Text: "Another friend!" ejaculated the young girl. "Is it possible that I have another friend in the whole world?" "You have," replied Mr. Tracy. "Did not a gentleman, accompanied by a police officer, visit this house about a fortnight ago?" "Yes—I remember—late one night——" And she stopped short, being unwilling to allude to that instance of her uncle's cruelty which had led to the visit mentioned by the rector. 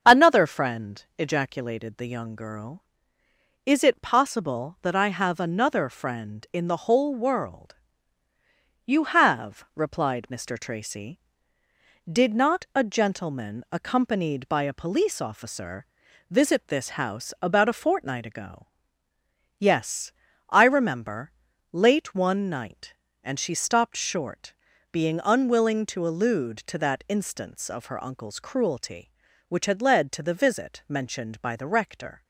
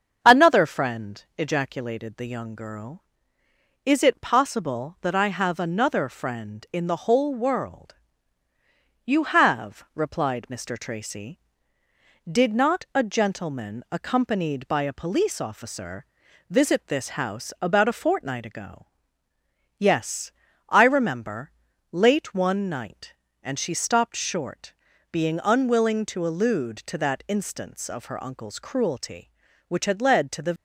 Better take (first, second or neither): first